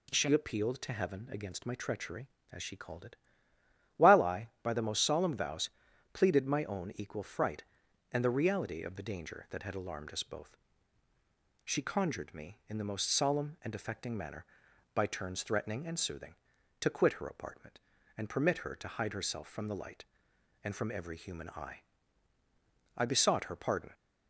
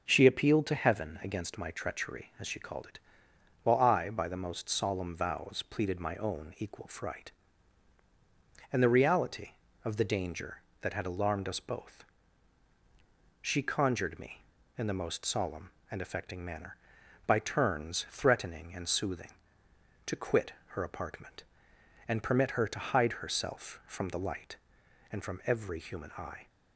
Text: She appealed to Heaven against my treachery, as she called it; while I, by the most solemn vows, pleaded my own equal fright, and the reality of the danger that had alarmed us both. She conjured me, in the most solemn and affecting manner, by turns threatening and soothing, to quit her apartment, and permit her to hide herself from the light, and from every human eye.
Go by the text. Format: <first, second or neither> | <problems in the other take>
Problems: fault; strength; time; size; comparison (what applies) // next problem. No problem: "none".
second | goes on to say "I besought her pardon"; noticeable; from 22.9 s on; 0.98 s long